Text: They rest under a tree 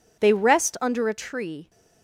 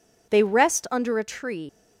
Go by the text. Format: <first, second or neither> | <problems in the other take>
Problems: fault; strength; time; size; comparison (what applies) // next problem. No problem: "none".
first | leaves "tree" unfinished; at 1.6 s; 105 ms